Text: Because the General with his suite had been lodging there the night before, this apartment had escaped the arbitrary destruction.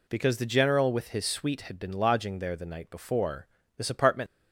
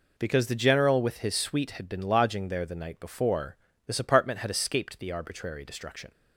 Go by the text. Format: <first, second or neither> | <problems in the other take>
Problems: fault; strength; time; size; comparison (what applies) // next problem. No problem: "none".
second | stops before "had escaped the arbitrary destruction"; at 4.2 s